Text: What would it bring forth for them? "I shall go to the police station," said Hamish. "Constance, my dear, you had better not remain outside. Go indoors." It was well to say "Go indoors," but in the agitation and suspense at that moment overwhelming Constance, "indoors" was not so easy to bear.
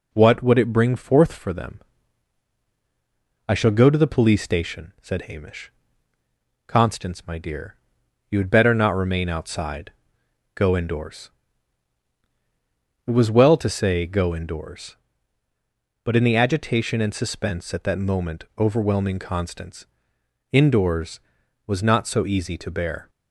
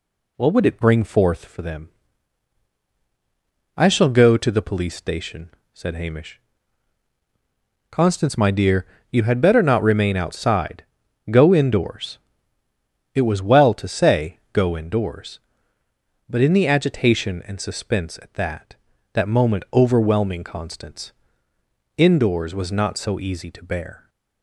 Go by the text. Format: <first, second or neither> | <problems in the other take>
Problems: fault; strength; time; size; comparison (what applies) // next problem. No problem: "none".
first | says "that" twice; at 19.1 s